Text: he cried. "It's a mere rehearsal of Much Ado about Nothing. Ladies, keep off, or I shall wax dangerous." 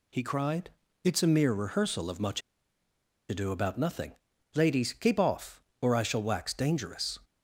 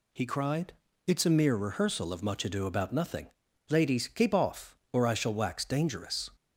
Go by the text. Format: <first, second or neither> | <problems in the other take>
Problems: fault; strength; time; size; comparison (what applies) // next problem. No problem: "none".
second | pauses between "Much" and "Ado"; noticeable; at 2.4 s; 0.88 s long